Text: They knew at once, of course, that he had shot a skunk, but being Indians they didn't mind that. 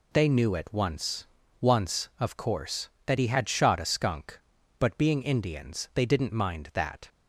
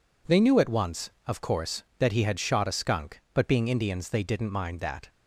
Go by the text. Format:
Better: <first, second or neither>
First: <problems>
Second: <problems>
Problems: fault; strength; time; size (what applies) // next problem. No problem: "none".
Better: second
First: says "once" twice; at 1.6 s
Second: none